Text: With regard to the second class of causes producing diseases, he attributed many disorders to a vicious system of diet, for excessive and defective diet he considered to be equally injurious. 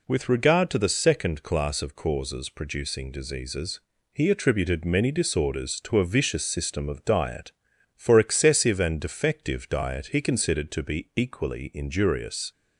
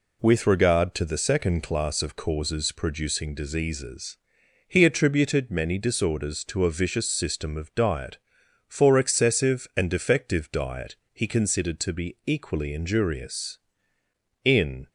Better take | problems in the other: first | pauses between "diet" and "he"; slight; at 10.9 s; 0.16 s long // goes on to say "In"; slight; from 14.4 s on; 0.46 s long

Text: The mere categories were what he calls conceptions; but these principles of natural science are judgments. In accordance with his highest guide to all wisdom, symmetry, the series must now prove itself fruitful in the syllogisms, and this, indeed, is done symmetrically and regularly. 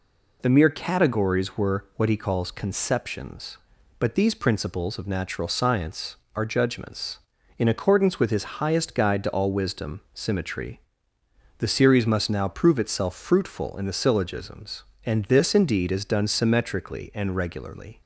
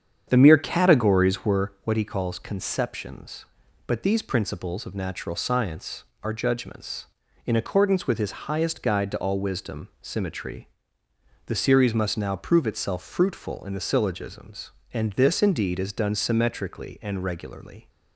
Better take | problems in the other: first | starts louder than the rest; strong; until 1.8 s; 8 dB

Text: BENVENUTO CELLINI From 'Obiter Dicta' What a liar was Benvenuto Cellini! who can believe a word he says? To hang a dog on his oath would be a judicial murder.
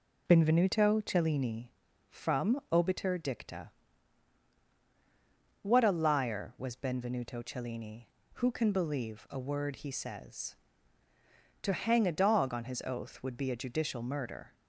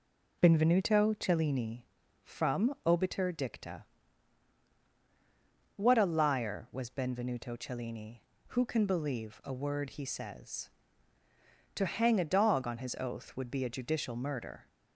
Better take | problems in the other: neither | pauses between "Dicta" and "What"; strong; the same in both

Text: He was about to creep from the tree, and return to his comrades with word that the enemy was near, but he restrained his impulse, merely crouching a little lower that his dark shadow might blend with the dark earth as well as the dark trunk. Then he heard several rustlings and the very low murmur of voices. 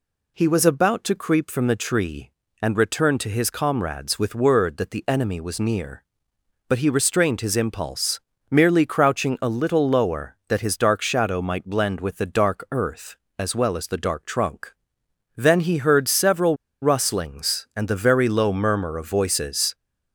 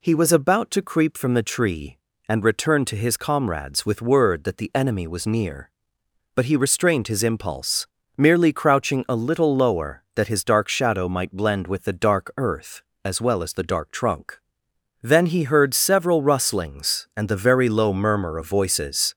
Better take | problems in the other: second | pauses between "several" and "rustlings"; slight; at 16.5 s; 0.26 s long

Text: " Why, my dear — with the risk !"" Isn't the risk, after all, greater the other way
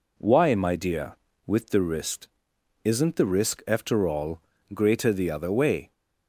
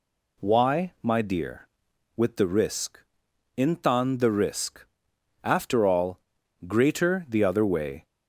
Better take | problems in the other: first | says "Intan" for "Isn't"; at 3.5 s

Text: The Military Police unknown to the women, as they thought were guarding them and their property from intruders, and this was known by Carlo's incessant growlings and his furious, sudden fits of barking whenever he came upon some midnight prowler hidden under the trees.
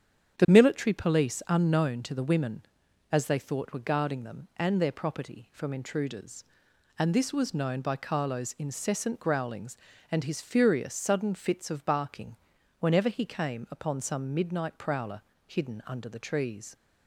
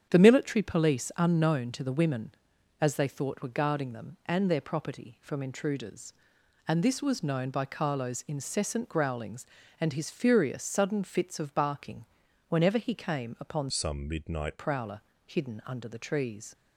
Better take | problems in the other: first | starts louder than the rest; strong; until 1.1 s; 8.5 dB; strong in the first // pauses between "barking" and "whenever"; at 12.0 s; 0.44 s long; also in the first // changes voice from "some" to "midnight"; from 13.6 to 14.5 s; 0.9 s long // pauses between "prowler" and "hidden"; slight; at 15.0 s; 0.26 s long; slight in the first

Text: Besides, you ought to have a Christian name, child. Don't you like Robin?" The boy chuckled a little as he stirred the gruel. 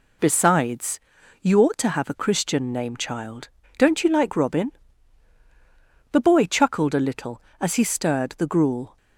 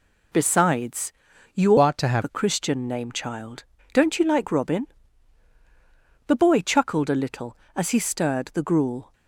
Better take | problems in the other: first | changes voice from "ought" to "have"; from 1.7 to 2.2 s; 0.5 s long

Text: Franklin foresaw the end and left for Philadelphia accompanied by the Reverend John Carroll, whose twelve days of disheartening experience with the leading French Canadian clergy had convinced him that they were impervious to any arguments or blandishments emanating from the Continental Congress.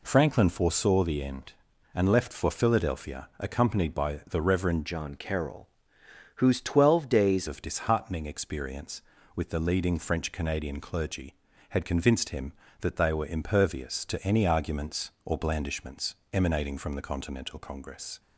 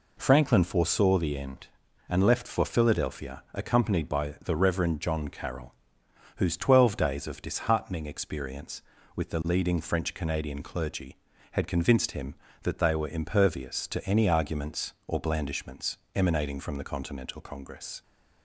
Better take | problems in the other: second | changes voice from "John" to "days"; from 4.8 to 7.4 s; 2.6 s long // pauses between "blandishments" and "emanating"; slight; at 16.1 s; 0.18 s long; slight in the second

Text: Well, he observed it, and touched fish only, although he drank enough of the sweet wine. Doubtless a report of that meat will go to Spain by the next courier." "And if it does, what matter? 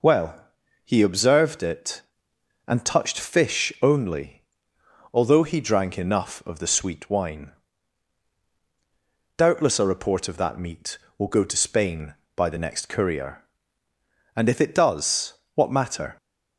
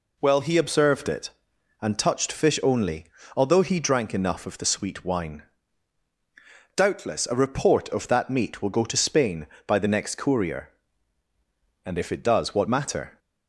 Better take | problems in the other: neither | none

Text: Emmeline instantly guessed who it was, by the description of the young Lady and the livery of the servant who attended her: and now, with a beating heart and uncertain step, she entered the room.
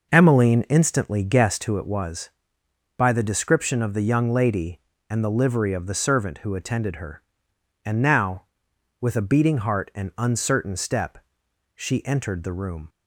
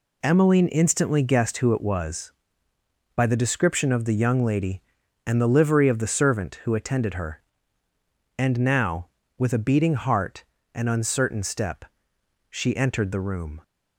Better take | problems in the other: second | starts louder than the rest; noticeable; until 1.8 s; 5.5 dB

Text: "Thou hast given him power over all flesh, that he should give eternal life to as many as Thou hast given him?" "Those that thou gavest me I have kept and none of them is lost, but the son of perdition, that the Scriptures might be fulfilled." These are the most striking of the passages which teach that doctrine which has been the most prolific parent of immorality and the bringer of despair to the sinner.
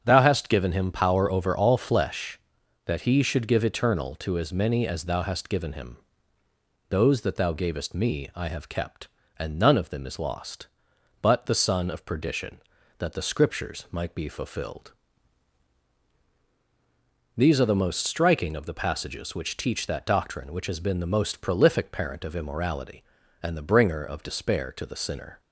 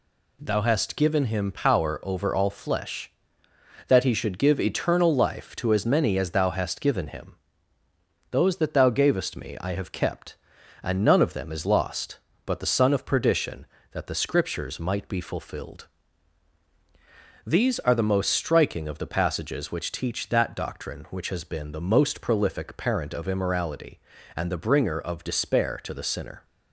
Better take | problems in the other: second | starts louder than the rest; strong; until 1.0 s; 7.5 dB // skips "life"; at 4.1 s

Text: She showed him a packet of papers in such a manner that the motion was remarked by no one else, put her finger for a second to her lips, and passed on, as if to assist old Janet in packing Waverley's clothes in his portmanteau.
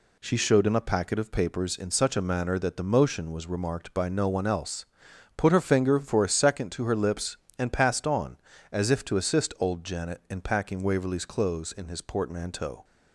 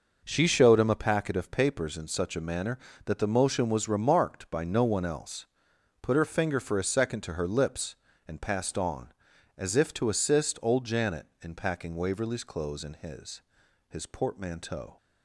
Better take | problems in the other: first | says "his" twice; at 13.8 s

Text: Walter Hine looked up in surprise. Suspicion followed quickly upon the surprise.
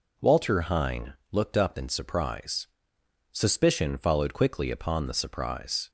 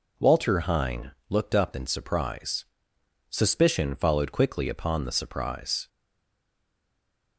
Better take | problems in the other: first | pauses between "Hine" and "looked"; slight; at 1.1 s; 0.18 s long; slight in the first // stays silent after the last word; noticeable; from 5.8 s on; 1.5 s long

